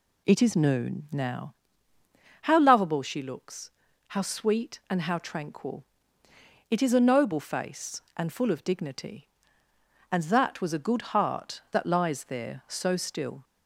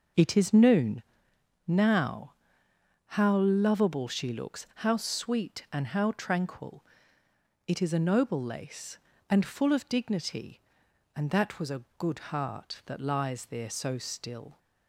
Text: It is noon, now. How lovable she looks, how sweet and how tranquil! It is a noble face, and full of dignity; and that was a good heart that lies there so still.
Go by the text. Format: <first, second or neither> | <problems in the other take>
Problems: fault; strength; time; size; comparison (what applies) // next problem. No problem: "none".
first | says "lace" for "face"; at 8.4 s // pauses between "a" and "good"; slight; at 11.8 s; 0.16 s long